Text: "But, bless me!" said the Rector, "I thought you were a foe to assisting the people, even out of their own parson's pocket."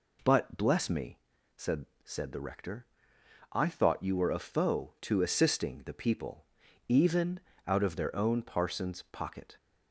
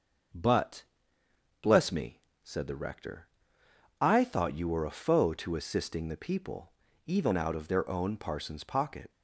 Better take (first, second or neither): second